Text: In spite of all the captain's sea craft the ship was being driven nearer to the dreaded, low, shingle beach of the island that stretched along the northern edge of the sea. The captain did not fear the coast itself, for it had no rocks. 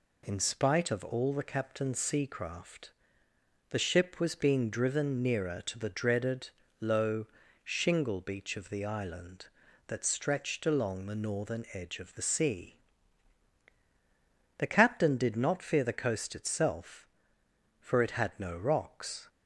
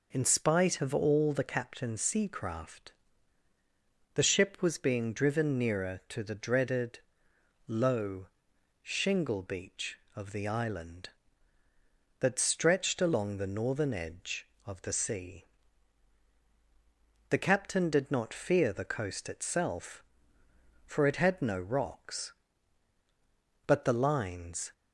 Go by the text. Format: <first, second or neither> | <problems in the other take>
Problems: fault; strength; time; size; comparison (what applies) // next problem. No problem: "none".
first | pauses between "craft" and "the"; at 2.9 s; 1.2 s long; noticeable in the first // goes on to say "But the lines"; noticeable; from 23.6 s on; 1.0 s long